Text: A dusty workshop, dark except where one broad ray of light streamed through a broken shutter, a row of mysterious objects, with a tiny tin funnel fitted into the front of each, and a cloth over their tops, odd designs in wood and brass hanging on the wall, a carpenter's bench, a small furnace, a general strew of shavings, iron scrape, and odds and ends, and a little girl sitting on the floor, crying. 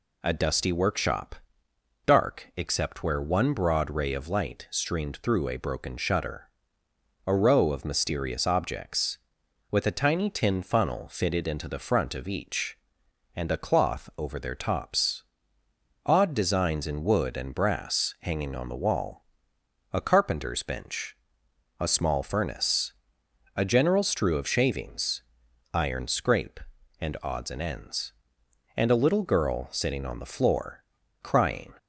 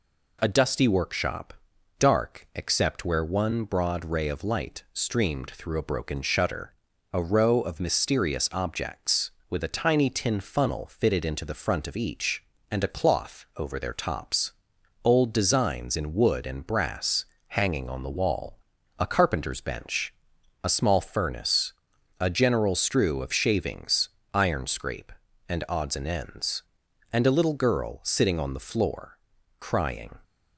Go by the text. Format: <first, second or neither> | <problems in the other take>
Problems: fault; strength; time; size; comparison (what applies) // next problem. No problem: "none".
first | says "old" for "odd"; at 15.0 s // pauses between "brass" and "hanging"; slight; at 17.2 s; 0.24 s long